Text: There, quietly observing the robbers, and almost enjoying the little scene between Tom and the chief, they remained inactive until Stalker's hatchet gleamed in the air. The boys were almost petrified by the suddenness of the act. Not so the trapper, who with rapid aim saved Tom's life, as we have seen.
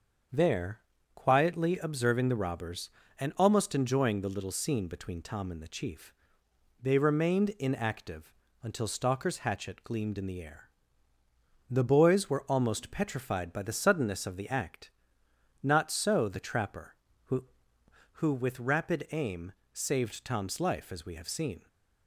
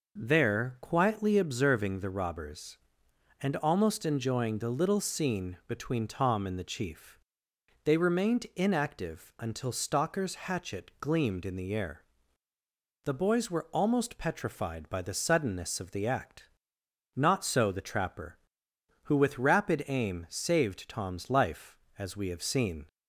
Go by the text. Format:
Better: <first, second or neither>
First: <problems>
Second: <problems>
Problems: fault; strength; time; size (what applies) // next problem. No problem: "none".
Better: second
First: starts louder than the rest; until 1.6 s; 7 dB // pauses between "inactive" and "until"; slight; at 8.3 s; 0.28 s long // says "who" twice; at 18.1 s // pauses between "aim" and "saved"; slight; at 19.5 s; 0.20 s long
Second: none